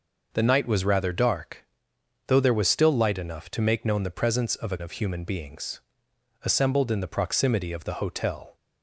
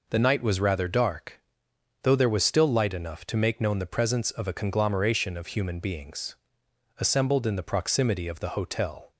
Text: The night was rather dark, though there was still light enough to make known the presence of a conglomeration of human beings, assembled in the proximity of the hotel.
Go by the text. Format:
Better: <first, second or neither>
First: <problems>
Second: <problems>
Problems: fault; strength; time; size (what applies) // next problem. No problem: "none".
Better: second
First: skips "conglomeration"; at 4.7 s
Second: none